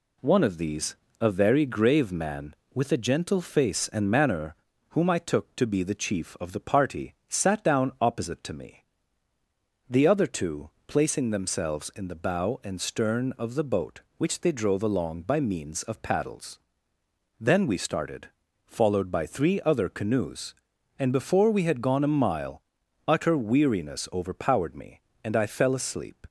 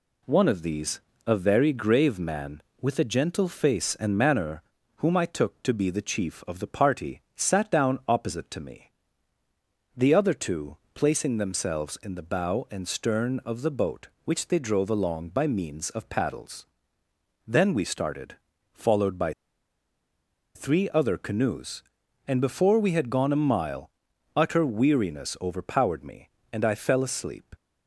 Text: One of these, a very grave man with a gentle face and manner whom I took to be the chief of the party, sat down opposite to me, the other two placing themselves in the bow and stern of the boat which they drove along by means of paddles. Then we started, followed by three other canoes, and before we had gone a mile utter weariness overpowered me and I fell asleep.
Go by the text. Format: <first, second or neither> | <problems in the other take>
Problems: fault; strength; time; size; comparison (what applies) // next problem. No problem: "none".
first | pauses between "manner" and "whom"; slight; at 4.6 s; 0.36 s long; slight in the first // pauses between "two" and "placing"; slight; at 10.7 s; 0.18 s long; slight in the first // pauses between "by" and "three"; at 19.3 s; 1.2 s long // pauses between "mile" and "utter"; at 23.9 s; 0.44 s long; also in the first